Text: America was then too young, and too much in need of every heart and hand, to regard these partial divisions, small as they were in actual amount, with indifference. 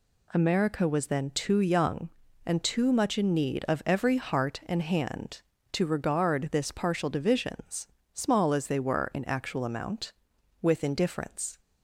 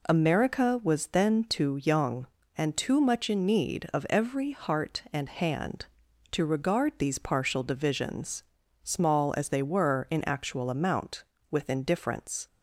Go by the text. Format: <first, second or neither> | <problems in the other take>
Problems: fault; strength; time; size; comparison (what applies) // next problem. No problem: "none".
second | says "this" for "these"; at 6.5 s